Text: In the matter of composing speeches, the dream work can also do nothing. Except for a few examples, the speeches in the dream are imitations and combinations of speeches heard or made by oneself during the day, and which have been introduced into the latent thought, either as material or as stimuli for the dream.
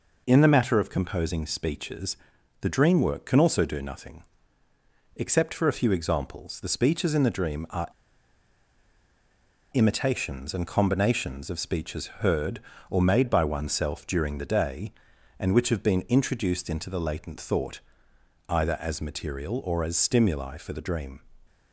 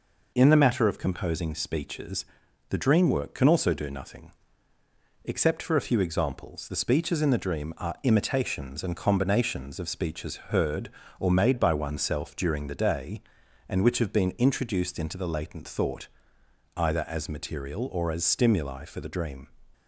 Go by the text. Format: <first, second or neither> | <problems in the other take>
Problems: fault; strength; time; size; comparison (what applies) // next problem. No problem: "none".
second | pauses between "are" and "imitations"; strong; at 7.8 s; 1.8 s long